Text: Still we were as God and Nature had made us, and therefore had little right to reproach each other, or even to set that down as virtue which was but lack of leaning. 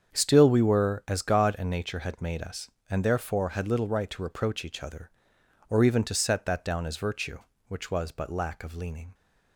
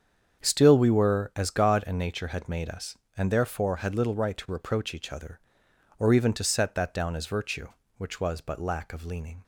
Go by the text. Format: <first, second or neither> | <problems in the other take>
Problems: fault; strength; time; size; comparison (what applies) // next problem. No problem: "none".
neither | starts louder than the rest; strong; the same in both